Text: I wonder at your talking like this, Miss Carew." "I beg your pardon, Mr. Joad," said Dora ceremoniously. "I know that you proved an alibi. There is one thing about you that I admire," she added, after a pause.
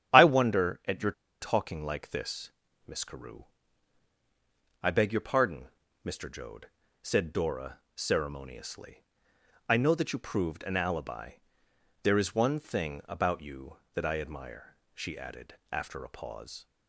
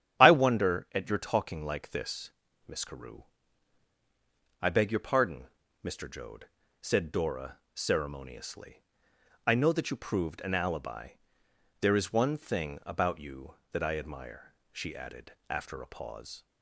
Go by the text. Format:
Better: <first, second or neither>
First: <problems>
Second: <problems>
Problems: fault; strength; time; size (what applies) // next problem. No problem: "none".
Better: second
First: starts louder than the rest; strong; until 1.4 s; 10 dB // pauses between "your" and "talking"; slight; at 1.1 s; 0.28 s long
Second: starts louder than the rest; strong; until 1.2 s; 10 dB